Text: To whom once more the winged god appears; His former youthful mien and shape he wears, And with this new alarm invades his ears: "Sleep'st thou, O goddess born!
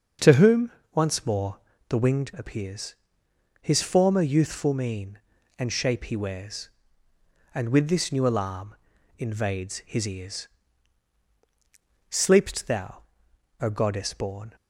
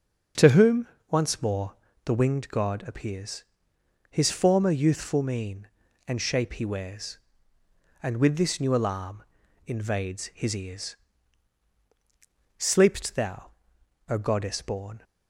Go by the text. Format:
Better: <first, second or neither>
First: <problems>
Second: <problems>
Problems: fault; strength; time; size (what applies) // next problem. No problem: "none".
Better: second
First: starts louder than the rest; until 1.4 s; 7 dB // pauses between "whom" and "once"; slight; at 0.6 s; 0.24 s long // pauses between "more" and "the"; slight; at 1.5 s; 0.28 s long // skips "god"; at 2.3 s // pauses between "alarm" and "invades"; at 8.7 s; 0.42 s long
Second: starts louder than the rest; until 1.5 s; 6.5 dB // pauses between "whom" and "once"; slight; at 0.8 s; 0.24 s long // pauses between "more" and "the"; slight; at 1.7 s; 0.28 s long // pauses between "alarm" and "invades"; at 9.2 s; 0.42 s long